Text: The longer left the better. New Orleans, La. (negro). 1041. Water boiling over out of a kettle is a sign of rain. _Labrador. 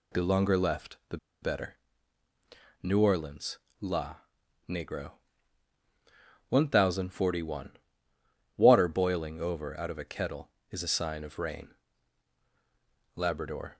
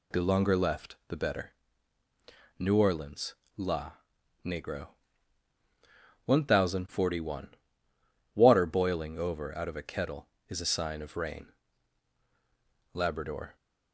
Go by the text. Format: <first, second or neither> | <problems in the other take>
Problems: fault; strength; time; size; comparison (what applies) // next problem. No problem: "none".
second | pauses between "the" and "better"; slight; at 1.1 s; 0.25 s long